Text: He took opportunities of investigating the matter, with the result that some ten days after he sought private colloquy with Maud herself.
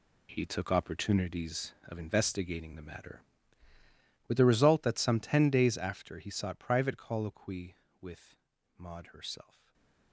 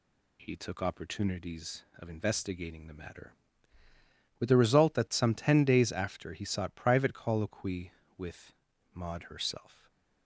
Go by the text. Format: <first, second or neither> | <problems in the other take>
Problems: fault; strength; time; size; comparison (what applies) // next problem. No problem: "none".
second | gets quieter; strong; throughout; 11.5 dB // pauses between "with" and "Maud"; at 8.3 s; 0.42 s long; also in the second // stays silent after the last word; slight; from 9.4 s on; 0.7 s long; slight in the second